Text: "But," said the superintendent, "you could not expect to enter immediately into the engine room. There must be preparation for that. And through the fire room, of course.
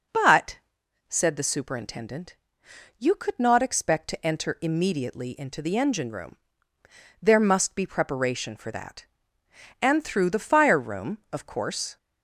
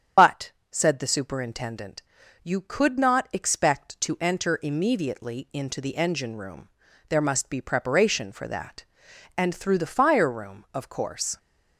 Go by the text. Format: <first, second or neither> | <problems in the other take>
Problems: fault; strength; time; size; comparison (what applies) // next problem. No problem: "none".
first | loses the start of "But"; at 0.1 s; 65 ms // starts louder than the rest; strong; until 1.4 s; 8.5 dB